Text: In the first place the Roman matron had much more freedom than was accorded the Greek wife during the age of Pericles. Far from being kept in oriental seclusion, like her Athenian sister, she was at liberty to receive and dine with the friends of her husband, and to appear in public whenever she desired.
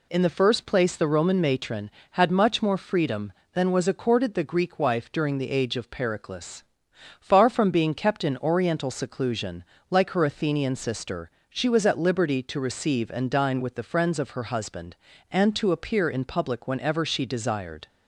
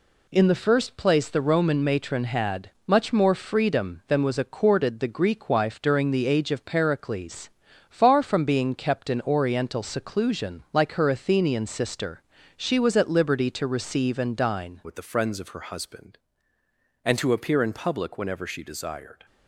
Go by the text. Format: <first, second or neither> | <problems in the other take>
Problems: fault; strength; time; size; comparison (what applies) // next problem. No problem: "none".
first | pauses between "had" and "much"; slight; at 2.6 s; 0.16 s long // changes voice at "with"; from 14.8 s on; 4.4 s long